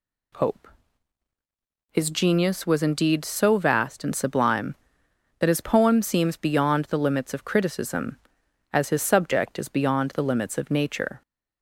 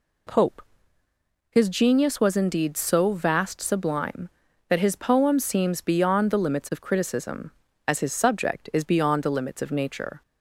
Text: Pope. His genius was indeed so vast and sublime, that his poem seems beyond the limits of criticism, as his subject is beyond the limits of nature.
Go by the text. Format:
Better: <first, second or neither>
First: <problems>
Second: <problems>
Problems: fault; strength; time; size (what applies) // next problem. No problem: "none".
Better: first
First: none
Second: skips "and"; at 3.5 s